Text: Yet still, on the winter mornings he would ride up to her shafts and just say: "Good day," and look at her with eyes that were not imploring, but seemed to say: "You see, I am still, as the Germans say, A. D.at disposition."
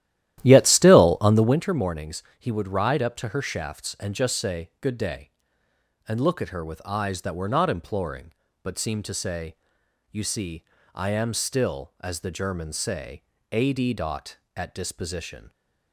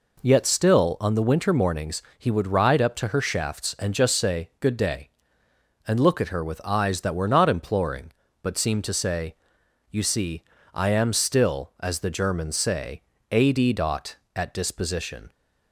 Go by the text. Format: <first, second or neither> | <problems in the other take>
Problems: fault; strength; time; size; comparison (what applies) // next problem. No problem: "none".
second | starts louder than the rest; strong; until 1.6 s; 13 dB // pauses between "mornings" and "he"; slight; at 2.2 s; 0.16 s long; slight in the second